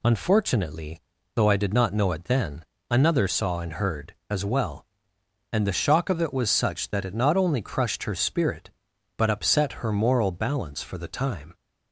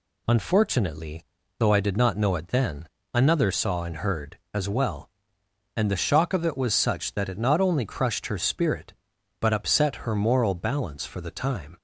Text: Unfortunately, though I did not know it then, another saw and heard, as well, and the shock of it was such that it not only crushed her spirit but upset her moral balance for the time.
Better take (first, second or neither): neither